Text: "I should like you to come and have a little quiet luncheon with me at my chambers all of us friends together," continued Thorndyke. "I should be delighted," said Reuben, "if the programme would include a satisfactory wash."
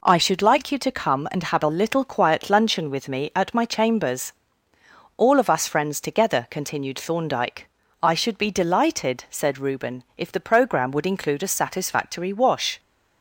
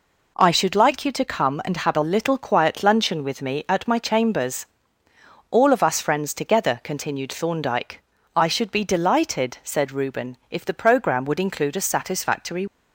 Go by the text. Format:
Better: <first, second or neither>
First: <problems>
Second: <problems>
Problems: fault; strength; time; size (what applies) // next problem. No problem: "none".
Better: first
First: pauses between "chambers" and "all"; noticeable; at 4.3 s; 0.86 s long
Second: pauses between "chambers" and "all"; noticeable; at 4.6 s; 0.86 s long // stops before "wash"; at 12.6 s